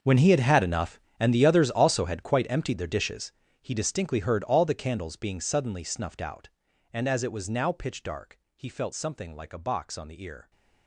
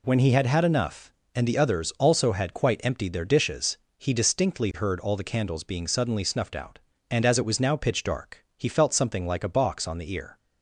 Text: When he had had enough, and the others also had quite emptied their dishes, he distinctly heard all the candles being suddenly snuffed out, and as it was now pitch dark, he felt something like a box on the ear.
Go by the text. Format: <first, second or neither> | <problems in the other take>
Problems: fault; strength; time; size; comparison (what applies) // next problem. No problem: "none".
second | gets quieter; strong; throughout; 17.5 dB